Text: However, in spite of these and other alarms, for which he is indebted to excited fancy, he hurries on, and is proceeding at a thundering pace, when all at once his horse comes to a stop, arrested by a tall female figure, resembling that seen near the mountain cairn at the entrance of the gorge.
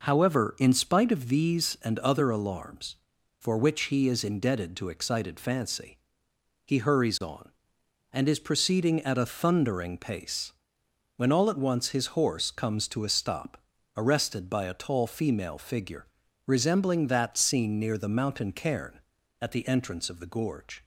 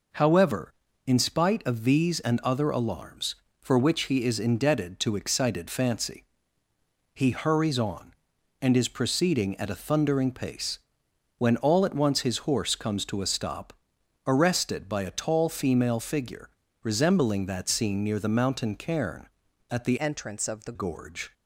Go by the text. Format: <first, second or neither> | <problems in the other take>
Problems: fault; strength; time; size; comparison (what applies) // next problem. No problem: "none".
first | changes voice from "entrance" to "the"; from 19.9 to 20.7 s; 0.8 s long